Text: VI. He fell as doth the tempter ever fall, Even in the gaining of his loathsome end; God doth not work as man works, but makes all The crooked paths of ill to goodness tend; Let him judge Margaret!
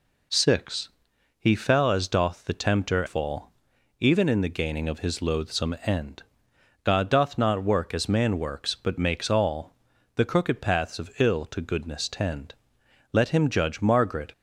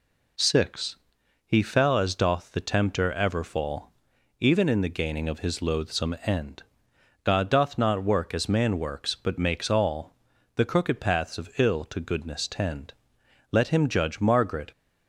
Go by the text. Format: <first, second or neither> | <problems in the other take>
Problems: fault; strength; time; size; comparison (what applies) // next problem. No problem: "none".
second | skips "ever"; at 3.0 s // pauses between "all" and "The"; at 9.7 s; 0.38 s long; also in the second